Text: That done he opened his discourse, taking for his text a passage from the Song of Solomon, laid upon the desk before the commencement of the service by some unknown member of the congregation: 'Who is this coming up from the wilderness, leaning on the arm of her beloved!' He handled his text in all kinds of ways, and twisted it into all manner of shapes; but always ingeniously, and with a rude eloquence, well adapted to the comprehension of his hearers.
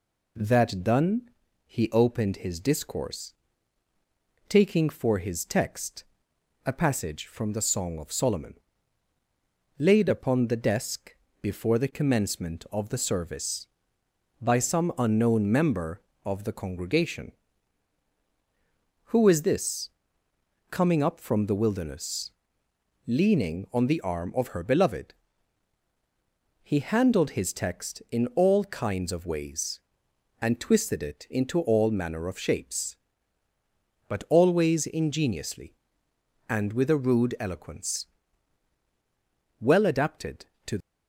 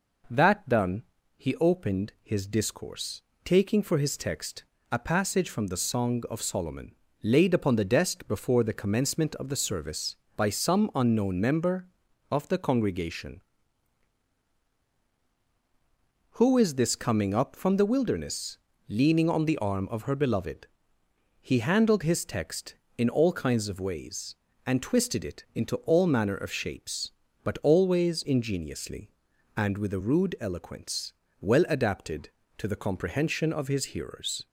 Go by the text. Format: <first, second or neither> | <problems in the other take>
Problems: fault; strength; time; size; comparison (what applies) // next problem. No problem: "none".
second | pauses between "done" and "he"; slight; at 1.3 s; 0.36 s long; slight in the second // pauses between "text" and "a"; noticeable; at 6.0 s; 0.62 s long; slight in the second // pauses between "desk" and "before"; slight; at 11.1 s; 0.24 s long // pauses between "this" and "coming"; noticeable; at 19.8 s; 0.80 s long // stops before "the comprehension of his hearers"; at 40.8 s